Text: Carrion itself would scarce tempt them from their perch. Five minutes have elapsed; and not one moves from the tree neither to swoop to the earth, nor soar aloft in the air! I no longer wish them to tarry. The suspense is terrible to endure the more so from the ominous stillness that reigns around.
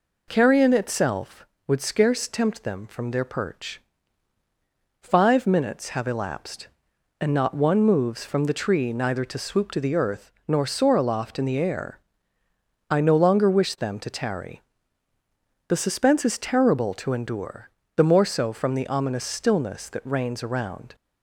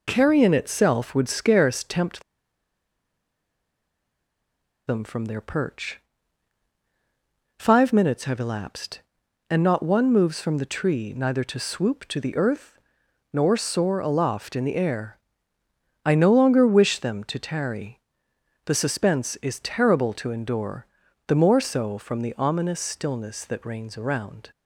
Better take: first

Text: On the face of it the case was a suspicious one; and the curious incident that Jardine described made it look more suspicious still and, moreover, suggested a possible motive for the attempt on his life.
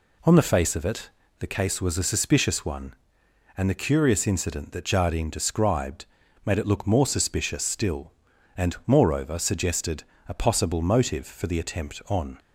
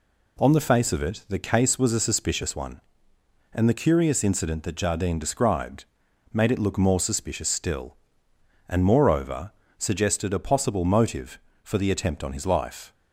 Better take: second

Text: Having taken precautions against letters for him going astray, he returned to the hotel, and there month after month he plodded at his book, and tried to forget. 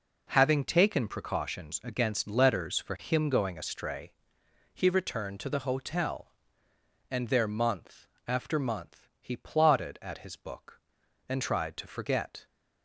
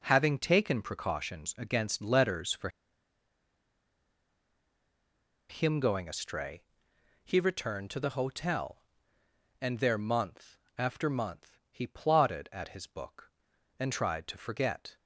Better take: first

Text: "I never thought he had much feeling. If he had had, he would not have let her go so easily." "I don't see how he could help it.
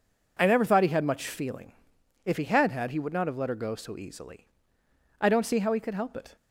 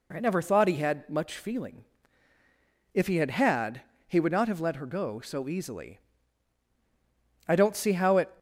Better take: first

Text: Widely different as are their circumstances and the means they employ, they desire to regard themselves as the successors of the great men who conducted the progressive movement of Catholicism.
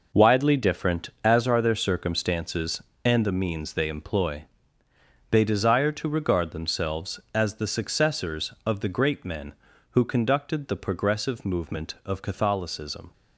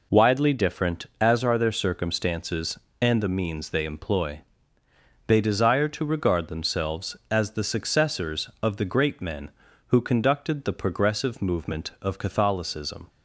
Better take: second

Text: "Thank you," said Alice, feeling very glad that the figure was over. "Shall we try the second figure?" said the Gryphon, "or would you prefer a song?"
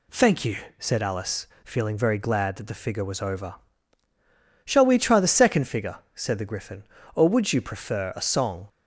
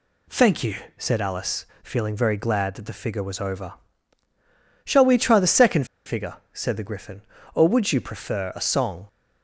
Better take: first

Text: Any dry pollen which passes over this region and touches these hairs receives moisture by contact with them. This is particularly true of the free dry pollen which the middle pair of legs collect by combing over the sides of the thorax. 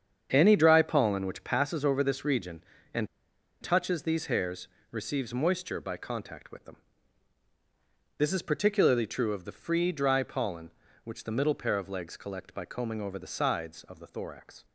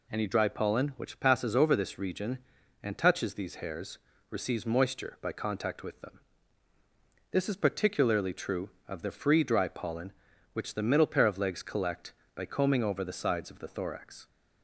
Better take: second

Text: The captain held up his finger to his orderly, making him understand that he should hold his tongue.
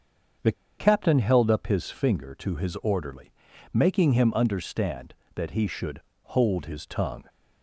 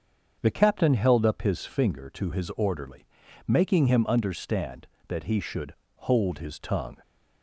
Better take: second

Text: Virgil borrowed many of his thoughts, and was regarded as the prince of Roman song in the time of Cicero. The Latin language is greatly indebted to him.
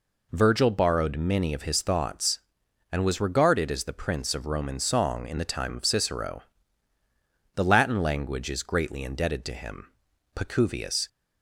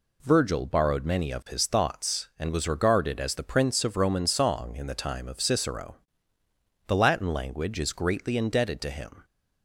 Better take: second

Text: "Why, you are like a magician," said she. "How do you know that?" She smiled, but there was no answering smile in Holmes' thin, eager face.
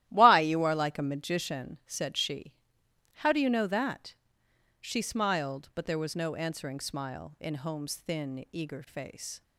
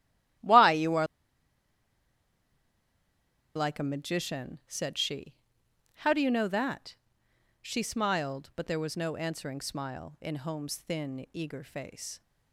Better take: first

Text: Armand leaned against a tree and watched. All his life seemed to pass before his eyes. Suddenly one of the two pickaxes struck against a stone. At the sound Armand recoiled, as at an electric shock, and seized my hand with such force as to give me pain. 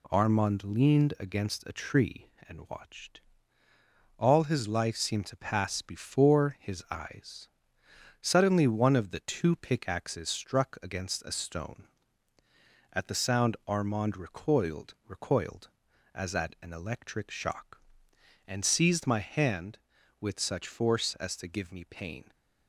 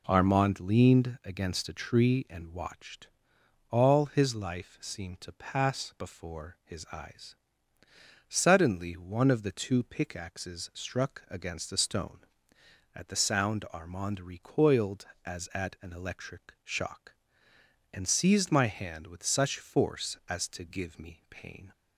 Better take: second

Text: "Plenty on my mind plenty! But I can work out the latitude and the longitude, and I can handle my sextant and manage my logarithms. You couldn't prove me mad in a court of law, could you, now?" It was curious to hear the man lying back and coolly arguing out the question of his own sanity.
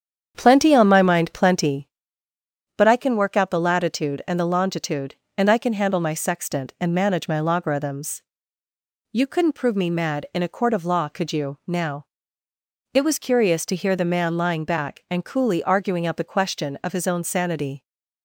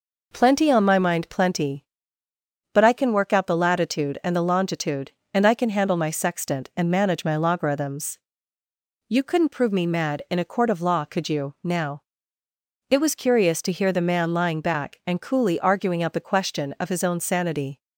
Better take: second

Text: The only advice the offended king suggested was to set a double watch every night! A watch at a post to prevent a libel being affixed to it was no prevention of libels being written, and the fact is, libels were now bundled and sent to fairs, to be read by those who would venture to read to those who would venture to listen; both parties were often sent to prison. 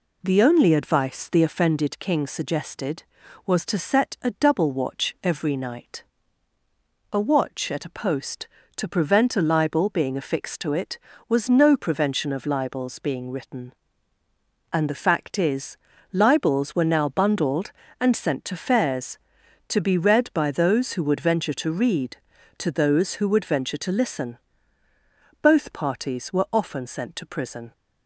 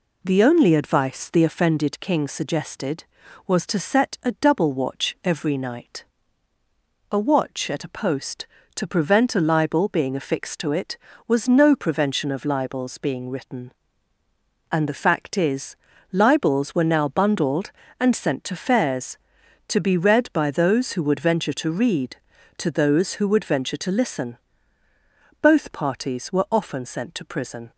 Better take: neither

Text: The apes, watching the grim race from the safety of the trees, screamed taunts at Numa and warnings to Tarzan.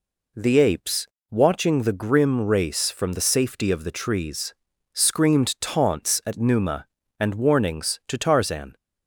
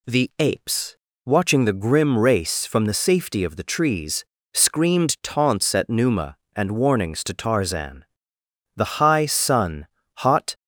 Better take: first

